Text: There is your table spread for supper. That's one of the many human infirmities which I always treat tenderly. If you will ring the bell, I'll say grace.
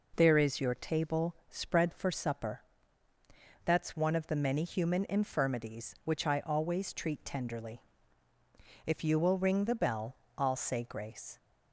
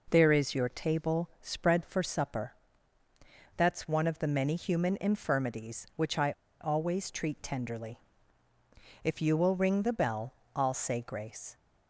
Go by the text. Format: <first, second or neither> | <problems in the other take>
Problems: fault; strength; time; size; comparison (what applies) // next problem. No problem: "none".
first | pauses between "I" and "always"; slight; at 6.3 s; 0.28 s long